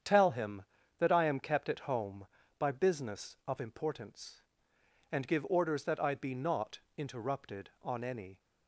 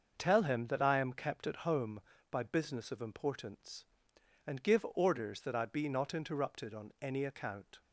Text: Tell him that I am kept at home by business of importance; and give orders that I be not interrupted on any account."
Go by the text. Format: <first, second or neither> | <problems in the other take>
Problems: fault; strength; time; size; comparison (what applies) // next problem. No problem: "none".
second | starts louder than the rest; strong; until 1.3 s; 8 dB; also in the second // pauses between "not" and "interrupted"; slight; at 6.7 s; 0.18 s long // stops before "account"; at 8.3 s